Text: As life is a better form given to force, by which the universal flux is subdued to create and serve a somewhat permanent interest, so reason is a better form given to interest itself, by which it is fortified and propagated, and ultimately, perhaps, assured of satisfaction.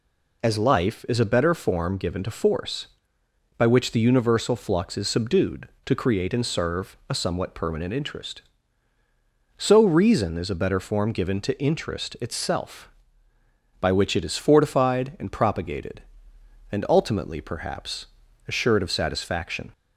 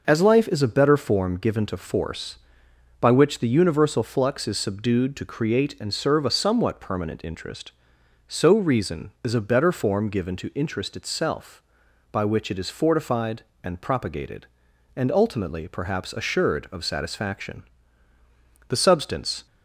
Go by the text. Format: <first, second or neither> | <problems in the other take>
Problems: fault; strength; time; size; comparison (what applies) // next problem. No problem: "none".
first | starts louder than the rest; noticeable; until 1.0 s; 6 dB // goes on to say "The substance"; noticeable; from 18.6 s on; 0.78 s long